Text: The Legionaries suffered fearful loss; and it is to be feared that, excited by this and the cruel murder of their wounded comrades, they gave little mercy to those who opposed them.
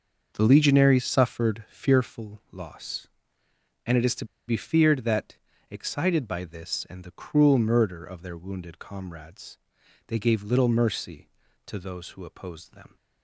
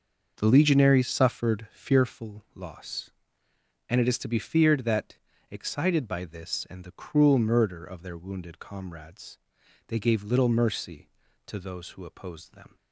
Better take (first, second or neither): second